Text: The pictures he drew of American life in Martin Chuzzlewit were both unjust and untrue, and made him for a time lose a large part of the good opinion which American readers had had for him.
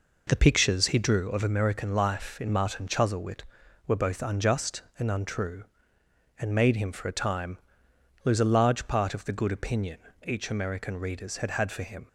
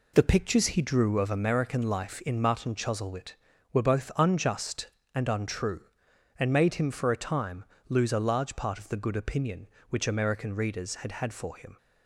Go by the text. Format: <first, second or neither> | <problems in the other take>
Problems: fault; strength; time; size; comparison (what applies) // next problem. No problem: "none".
second | pauses between "time" and "lose"; noticeable; at 7.5 s; 0.66 s long; slight in the second // says "each" for "which"; at 10.2 s